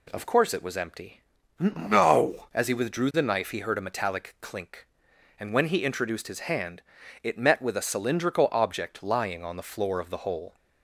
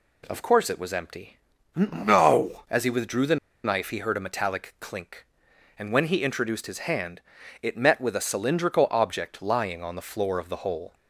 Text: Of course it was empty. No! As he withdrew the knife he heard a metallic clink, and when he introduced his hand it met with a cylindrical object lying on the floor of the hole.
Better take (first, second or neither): first